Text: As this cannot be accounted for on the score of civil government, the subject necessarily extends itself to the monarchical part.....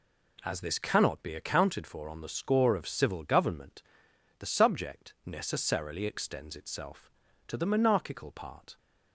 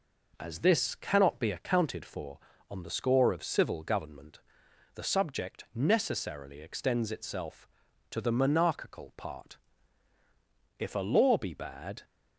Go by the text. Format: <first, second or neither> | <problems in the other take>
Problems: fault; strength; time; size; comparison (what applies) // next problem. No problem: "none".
first | goes on to say "If a law be bad"; noticeable; from 10.7 s on; 1.2 s long